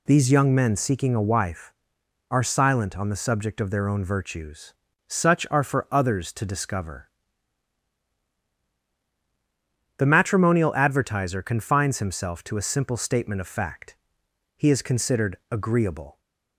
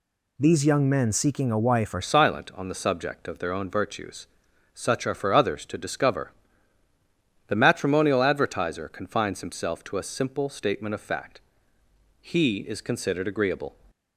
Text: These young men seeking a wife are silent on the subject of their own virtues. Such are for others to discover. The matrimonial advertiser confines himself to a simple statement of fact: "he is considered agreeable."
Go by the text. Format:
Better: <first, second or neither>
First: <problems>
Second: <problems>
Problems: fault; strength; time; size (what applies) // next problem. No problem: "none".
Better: first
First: none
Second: changes voice at "silent"; from 2.0 s on; 11.7 s long